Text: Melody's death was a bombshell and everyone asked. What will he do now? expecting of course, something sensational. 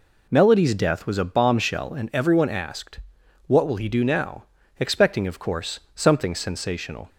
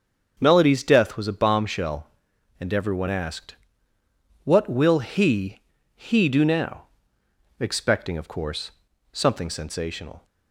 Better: first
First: none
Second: starts louder than the rest; until 1.3 s; 6.5 dB // says "he" twice; at 5.9 s

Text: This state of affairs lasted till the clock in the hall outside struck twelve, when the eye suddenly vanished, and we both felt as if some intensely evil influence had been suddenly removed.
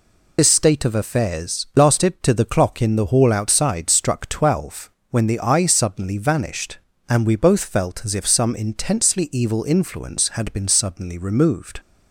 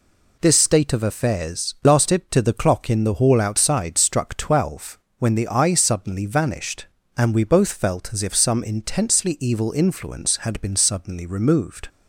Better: second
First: loses the start of "This"; at 0.3 s; 70 ms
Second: none

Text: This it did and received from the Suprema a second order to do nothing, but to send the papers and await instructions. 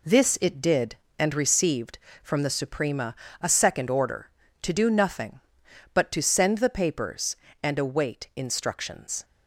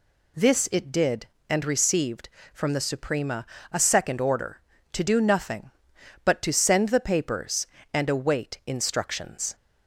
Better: second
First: gets quieter; throughout; 7 dB // pauses between "Suprema" and "a"; slight; at 3.1 s; 0.26 s long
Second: pauses between "Suprema" and "a"; slight; at 3.4 s; 0.26 s long

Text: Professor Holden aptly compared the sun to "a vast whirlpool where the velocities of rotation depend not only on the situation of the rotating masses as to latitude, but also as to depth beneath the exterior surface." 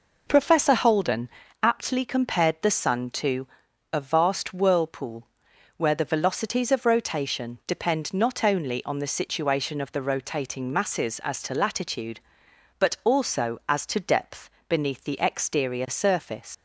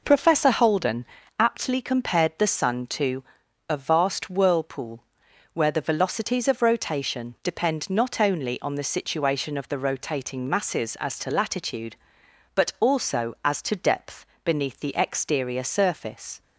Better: second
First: pauses between "Holden" and "aptly"; slight; at 1.2 s; 0.32 s long // pauses between "to" and "a"; noticeable; at 3.4 s; 0.46 s long // pauses between "whirlpool" and "where"; noticeable; at 5.2 s; 0.52 s long // pauses between "depth" and "beneath"; slight; at 14.4 s; 0.18 s long // leaves "surface" unfinished; at 16.5 s; 125 ms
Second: pauses between "Holden" and "aptly"; slight; at 1.0 s; 0.32 s long // pauses between "to" and "a"; noticeable; at 3.2 s; 0.46 s long // pauses between "whirlpool" and "where"; noticeable; at 5.0 s; 0.52 s long // pauses between "depth" and "beneath"; slight; at 14.2 s; 0.18 s long

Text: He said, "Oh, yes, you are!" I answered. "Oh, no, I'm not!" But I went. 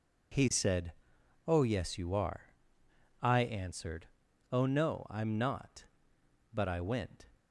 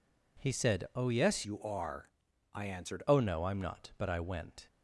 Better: first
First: none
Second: changes voice from "you" to "answered"; from 1.4 to 3.0 s; 1.6 s long

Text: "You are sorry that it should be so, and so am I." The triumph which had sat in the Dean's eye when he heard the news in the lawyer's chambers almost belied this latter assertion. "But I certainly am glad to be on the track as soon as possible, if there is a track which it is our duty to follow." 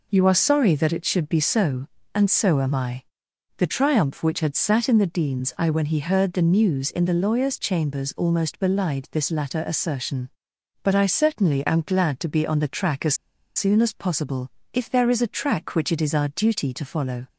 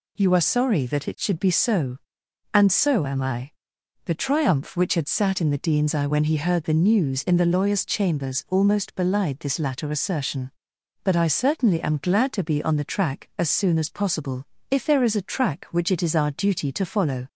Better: second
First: pauses between "as" and "soon"; at 13.1 s; 0.41 s long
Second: none

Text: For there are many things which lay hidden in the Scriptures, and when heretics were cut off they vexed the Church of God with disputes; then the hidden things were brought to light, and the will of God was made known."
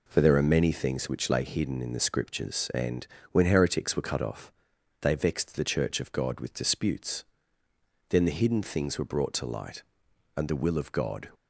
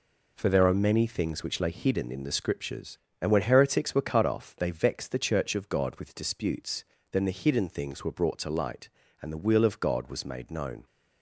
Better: second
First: pauses between "and" and "when"; slight; at 3.0 s; 0.28 s long // pauses between "off" and "they"; noticeable; at 4.5 s; 0.50 s long // stops before "was made known"; at 11.3 s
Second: none

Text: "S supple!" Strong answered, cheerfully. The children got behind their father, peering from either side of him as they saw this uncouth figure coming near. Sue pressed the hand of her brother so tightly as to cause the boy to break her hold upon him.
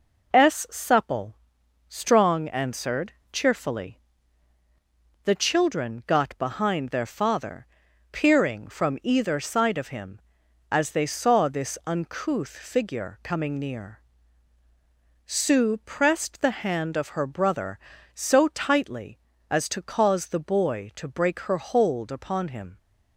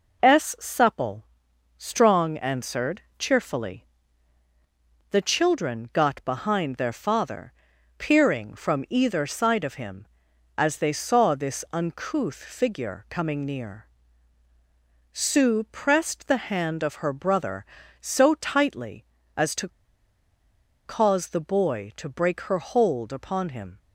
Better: first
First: none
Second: pauses between "to" and "cause"; at 19.6 s; 1.1 s long

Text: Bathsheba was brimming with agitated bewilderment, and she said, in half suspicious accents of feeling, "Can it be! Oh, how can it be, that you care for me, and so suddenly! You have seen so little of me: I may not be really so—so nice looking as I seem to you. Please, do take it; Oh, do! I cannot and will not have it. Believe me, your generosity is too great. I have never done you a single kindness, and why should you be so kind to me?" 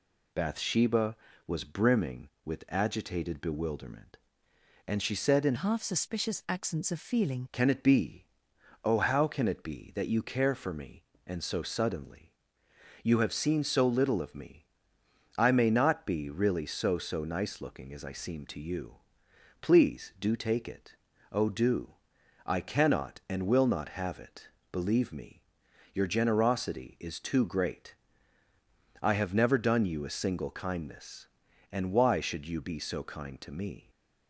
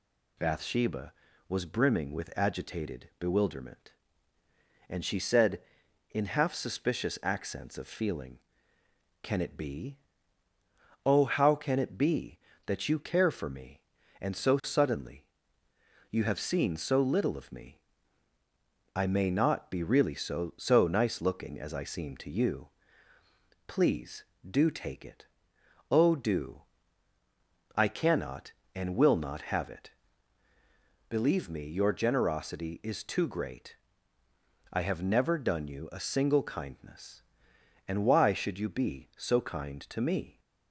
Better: second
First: changes voice from "half" to "feeling"; from 5.5 to 7.4 s; 1.9 s long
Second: none

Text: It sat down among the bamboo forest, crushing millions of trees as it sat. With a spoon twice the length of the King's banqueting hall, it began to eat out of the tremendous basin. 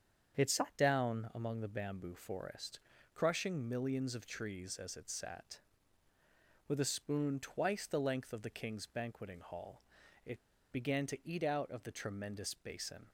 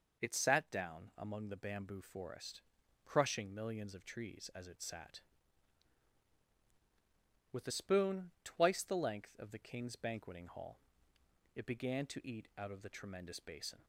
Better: second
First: starts louder than the rest; strong; until 1.4 s; 7.5 dB // pauses between "it" and "began"; slight; at 10.3 s; 0.33 s long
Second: none

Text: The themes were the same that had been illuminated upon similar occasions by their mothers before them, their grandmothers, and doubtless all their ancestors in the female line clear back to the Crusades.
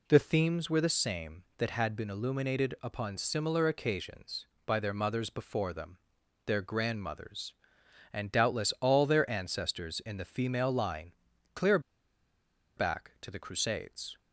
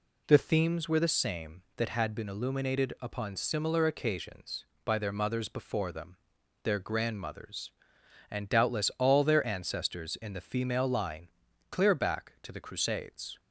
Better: second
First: pauses between "line" and "clear"; at 11.1 s; 0.42 s long // pauses between "clear" and "back"; noticeable; at 11.7 s; 0.97 s long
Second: pauses between "line" and "clear"; at 11.2 s; 0.42 s long

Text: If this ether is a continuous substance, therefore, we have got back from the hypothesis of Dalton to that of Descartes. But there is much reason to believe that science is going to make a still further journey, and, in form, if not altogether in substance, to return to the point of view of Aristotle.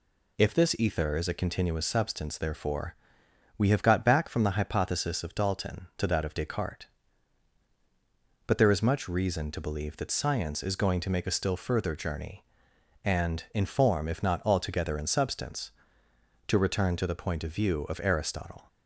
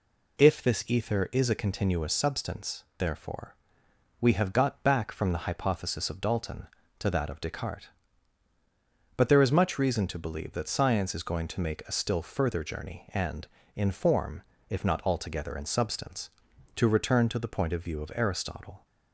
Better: neither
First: none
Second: none

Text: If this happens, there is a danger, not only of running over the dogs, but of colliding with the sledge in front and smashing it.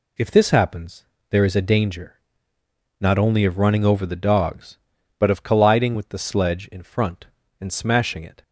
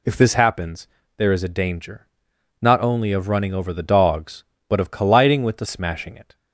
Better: first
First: none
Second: skips "sledge in front and"; at 5.6 s

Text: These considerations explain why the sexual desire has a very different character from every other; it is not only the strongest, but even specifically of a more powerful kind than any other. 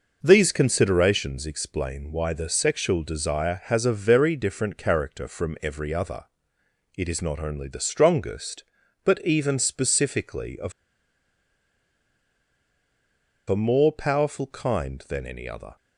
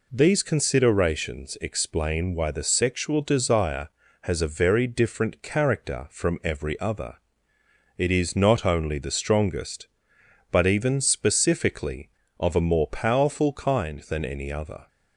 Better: second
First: pauses between "of" and "a"; strong; at 10.7 s; 2.7 s long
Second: none

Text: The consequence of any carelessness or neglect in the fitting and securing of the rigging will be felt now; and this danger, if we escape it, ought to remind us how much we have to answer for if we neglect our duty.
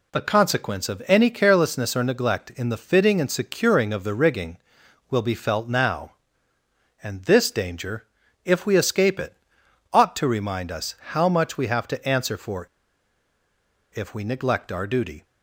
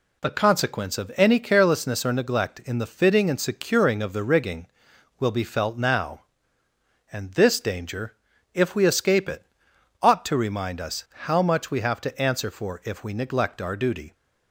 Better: second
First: pauses between "us" and "how"; slight; at 10.9 s; 0.16 s long // pauses between "for" and "if"; strong; at 12.6 s; 1.2 s long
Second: pauses between "us" and "how"; slight; at 11.0 s; 0.20 s long

